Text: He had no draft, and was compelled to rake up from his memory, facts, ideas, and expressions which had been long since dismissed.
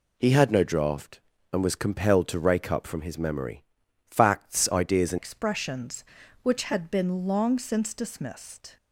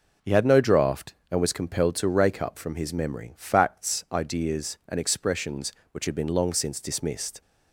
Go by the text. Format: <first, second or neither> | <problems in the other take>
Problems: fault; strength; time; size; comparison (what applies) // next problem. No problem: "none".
second | changes voice at "expressions"; from 5.1 s on; 3.6 s long